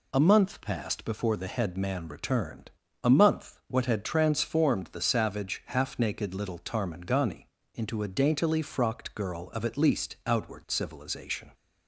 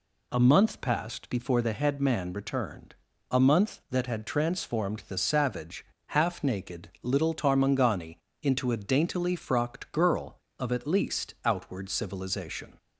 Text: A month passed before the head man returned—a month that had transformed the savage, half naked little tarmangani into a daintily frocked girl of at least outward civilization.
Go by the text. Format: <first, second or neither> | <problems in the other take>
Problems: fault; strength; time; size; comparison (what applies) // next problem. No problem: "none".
second | says "what" for "that"; at 3.6 s // pauses between "tarmangani" and "into"; slight; at 7.4 s; 0.26 s long; slight in the second